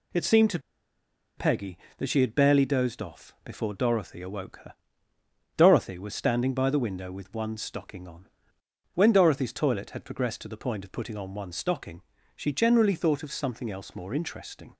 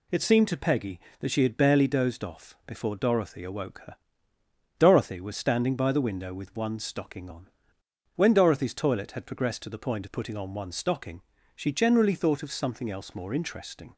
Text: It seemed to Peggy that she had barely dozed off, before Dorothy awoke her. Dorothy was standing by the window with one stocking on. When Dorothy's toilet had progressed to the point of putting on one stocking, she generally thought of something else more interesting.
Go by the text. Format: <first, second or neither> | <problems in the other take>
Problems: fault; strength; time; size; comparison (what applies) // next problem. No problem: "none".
second | pauses between "to" and "Peggy"; noticeable; at 0.5 s; 0.78 s long